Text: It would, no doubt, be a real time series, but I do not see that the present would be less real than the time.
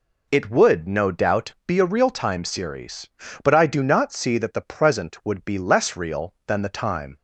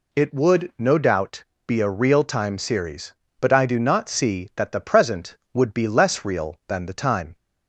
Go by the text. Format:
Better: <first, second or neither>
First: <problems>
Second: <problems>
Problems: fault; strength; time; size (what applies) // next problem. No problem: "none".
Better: neither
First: none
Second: none